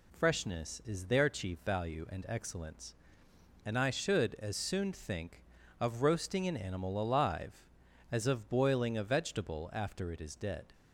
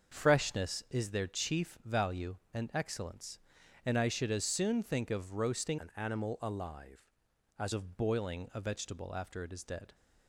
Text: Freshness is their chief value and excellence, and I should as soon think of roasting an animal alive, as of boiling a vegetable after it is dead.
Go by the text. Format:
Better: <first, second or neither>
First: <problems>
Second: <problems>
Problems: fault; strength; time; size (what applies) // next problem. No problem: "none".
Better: first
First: none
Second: starts louder than the rest; until 1.2 s; 6.5 dB // changes voice from "an" to "as"; from 5.7 to 7.7 s; 2.0 s long